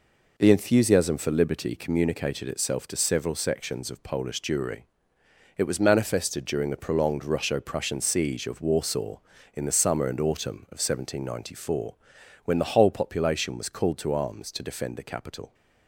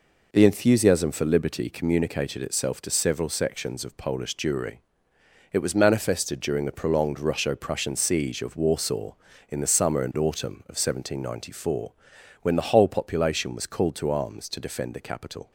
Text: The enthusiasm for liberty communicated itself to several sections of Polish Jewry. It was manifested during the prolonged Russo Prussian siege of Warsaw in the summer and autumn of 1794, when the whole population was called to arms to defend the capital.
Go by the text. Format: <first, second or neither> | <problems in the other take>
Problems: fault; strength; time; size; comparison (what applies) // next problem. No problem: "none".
neither | none